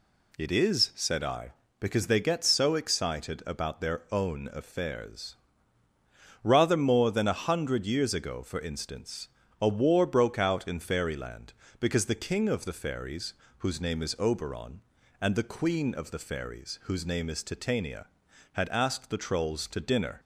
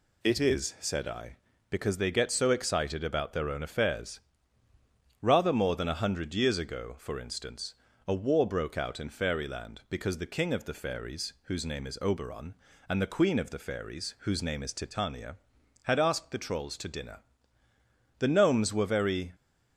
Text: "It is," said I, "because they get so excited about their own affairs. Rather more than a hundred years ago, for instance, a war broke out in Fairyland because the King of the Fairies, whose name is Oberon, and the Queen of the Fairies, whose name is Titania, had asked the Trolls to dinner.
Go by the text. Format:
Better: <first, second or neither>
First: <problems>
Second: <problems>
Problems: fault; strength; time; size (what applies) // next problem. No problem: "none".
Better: first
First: none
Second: goes on to say "The Gnomes were very"; noticeable; from 18.1 s on; 1.1 s long